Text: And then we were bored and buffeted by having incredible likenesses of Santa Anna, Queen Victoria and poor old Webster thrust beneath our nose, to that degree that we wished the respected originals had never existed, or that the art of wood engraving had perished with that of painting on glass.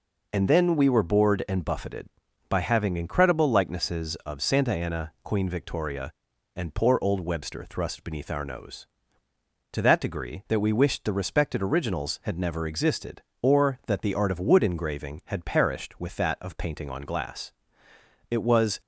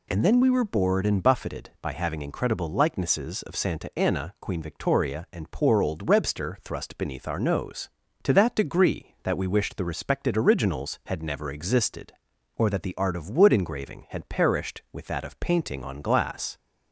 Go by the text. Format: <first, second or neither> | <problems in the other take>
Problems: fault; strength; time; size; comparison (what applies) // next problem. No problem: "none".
second | goes on to say "It was"; from 18.3 s on; 0.50 s long